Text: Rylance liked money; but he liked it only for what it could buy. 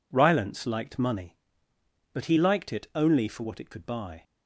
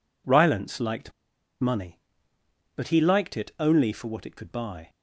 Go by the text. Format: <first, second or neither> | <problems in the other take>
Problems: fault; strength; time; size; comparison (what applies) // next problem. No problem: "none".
first | pauses between "liked" and "money"; noticeable; at 1.1 s; 0.49 s long